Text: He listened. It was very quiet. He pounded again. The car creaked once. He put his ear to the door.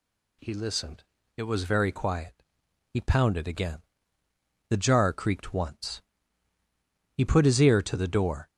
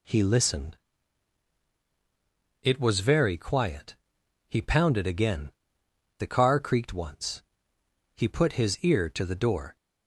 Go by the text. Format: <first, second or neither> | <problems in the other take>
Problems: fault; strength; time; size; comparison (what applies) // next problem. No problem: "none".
second | says "jar" for "car"; at 4.7 s